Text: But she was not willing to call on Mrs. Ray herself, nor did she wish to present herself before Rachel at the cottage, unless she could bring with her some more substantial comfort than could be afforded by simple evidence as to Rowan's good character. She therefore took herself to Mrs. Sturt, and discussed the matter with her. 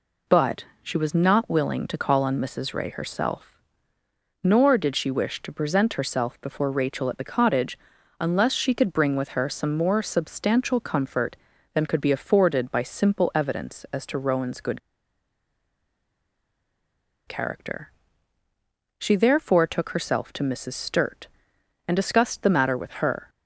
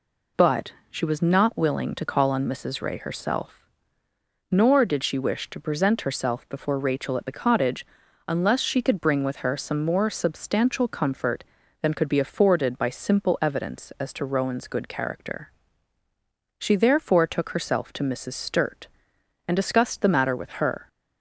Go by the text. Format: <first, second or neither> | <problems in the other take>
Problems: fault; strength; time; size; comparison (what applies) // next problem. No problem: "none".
second | pauses between "But" and "she"; slight; at 0.6 s; 0.18 s long; slight in the second // pauses between "good" and "character"; strong; at 14.7 s; 2.4 s long